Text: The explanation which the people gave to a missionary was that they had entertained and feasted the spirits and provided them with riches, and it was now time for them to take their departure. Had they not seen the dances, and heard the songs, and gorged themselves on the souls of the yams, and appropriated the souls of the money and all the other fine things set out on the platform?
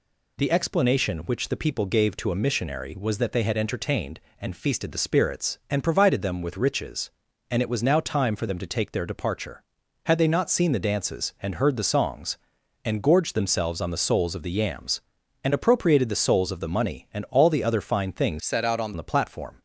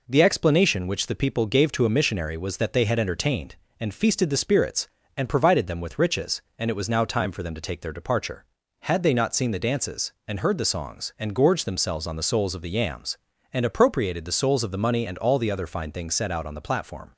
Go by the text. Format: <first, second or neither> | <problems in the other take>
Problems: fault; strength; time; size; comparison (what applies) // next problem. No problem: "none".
second | changes voice from "set" to "on"; from 18.3 to 18.9 s; 0.6 s long